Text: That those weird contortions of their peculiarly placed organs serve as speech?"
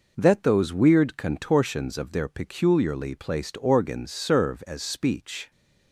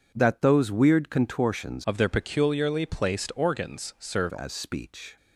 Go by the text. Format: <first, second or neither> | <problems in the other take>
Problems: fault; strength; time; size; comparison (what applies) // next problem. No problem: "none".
first | changes voice from "of" to "serve"; from 1.8 to 4.3 s; 2.5 s long